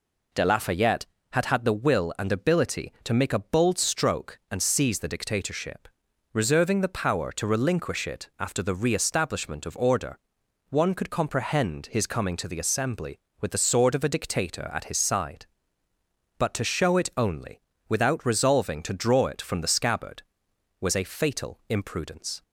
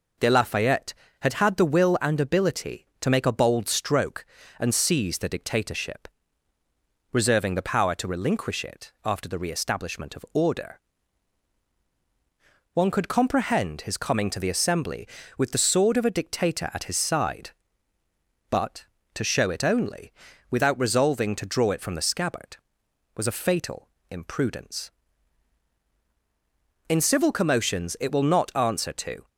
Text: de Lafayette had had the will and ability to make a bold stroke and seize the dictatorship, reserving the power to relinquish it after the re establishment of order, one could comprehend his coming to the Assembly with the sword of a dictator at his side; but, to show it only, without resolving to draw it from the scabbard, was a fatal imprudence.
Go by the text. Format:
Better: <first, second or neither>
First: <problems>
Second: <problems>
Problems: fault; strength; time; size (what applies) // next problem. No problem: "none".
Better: first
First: none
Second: pauses between "fatal" and "imprudence"; slight; at 23.8 s; 0.24 s long // goes on to say "In civil commotions it will not answer to"; strong; from 26.8 s on; 2.4 s long